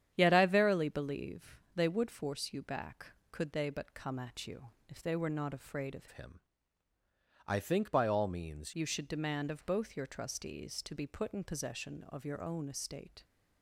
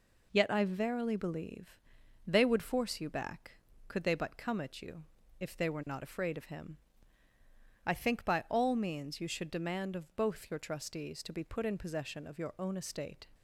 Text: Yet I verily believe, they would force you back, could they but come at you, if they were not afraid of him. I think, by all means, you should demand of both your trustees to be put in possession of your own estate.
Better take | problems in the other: second | starts louder than the rest; strong; until 1.1 s; 9.5 dB // changes voice from "him" to "means"; from 6.1 to 8.7 s; 2.6 s long

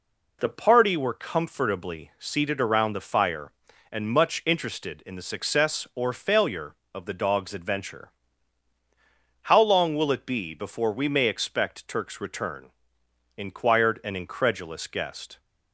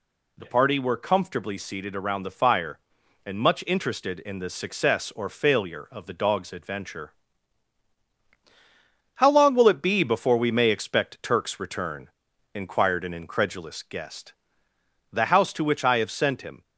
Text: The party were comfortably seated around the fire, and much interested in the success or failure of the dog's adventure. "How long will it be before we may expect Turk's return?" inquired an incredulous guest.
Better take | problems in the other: first | goes on to say "The house to which I have sent him"; from 15.0 s on; 1.5 s long

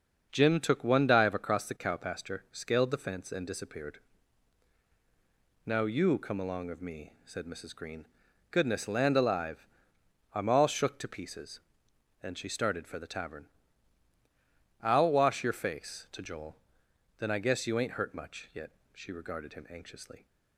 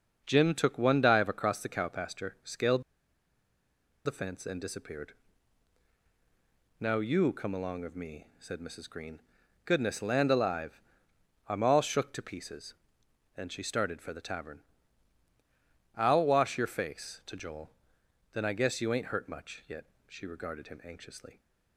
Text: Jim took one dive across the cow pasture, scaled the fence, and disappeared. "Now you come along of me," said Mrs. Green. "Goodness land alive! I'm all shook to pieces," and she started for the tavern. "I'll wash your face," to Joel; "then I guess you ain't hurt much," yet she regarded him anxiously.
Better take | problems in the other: first | starts louder than the rest; until 1.2 s; 6.5 dB; also in the first // pauses between "scaled" and "the"; at 2.8 s; 1.2 s long // pauses between "yet" and "she"; slight; at 19.8 s; 0.22 s long; slight in the first

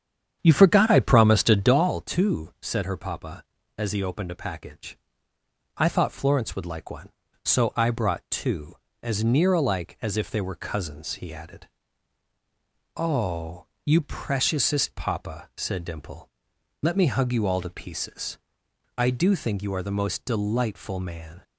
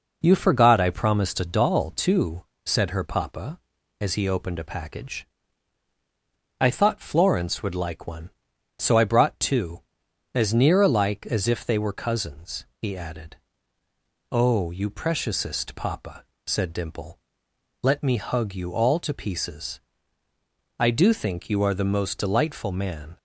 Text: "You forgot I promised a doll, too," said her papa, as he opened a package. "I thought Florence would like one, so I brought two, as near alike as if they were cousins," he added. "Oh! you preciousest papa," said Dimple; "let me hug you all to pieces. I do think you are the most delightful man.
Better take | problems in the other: second | starts louder than the rest; strong; until 1.8 s; 8.5 dB

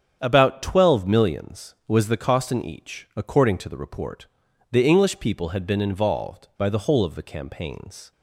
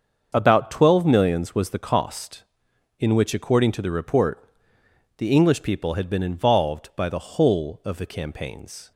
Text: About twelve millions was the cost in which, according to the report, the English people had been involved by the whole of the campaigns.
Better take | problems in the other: second | starts louder than the rest; strong; until 1.2 s; 7.5 dB; also in the second // says "each" for "which"; at 2.6 s

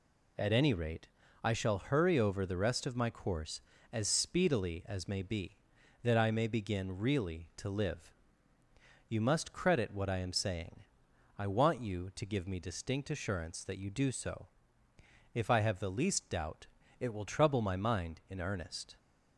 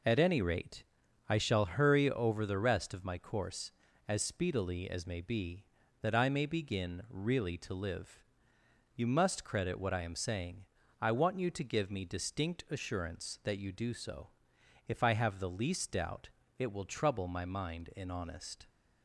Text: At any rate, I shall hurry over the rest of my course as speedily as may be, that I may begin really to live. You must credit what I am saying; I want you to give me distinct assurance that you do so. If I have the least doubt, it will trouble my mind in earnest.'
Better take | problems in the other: first | says "honest" for "earnest"; at 18.0 s

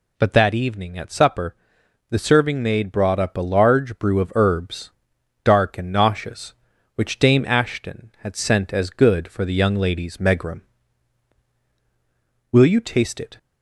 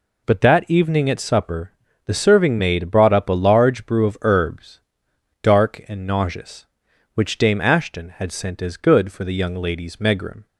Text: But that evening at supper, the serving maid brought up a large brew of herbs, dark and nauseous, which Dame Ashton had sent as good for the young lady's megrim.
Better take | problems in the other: second | goes on to say "Will you taste it"; noticeable; from 12.5 s on; 0.86 s long

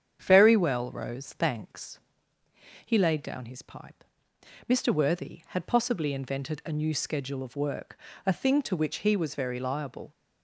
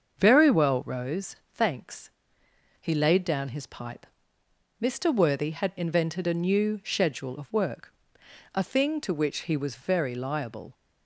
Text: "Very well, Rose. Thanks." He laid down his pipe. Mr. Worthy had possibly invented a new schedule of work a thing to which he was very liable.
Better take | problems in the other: first | starts louder than the rest; until 1.2 s; 6.5 dB; strong in the first // skips "possibly"; at 5.7 s // pauses between "work" and "a"; noticeable; at 7.9 s; 0.62 s long; slight in the first

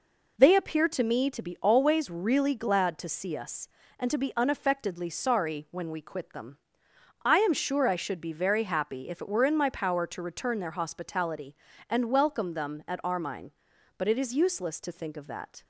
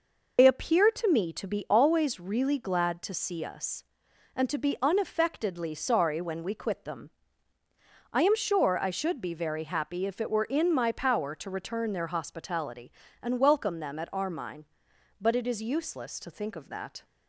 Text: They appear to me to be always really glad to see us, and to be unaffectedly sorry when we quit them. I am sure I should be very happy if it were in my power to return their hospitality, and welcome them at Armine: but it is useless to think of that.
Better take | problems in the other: first | loses the start of "They"; at 0.3 s; 65 ms

